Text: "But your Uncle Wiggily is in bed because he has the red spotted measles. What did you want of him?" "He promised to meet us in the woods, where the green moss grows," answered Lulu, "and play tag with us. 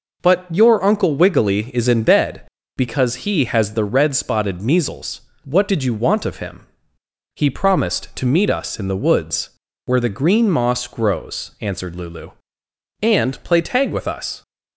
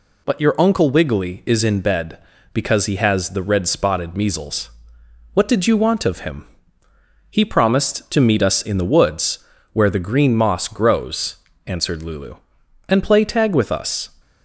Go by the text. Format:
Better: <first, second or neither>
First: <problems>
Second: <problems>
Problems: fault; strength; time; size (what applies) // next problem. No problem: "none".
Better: neither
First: none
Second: none